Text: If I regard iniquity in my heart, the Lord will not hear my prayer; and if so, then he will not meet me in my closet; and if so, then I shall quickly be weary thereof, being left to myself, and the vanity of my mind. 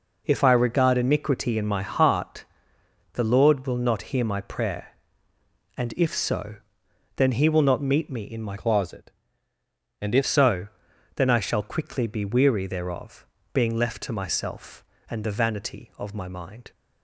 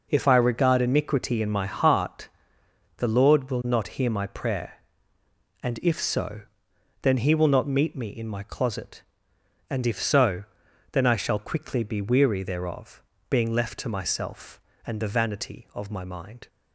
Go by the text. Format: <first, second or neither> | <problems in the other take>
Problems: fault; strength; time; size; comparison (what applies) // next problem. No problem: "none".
second | changes voice from "closet" to "if"; from 8.5 to 10.2 s; 1.7 s long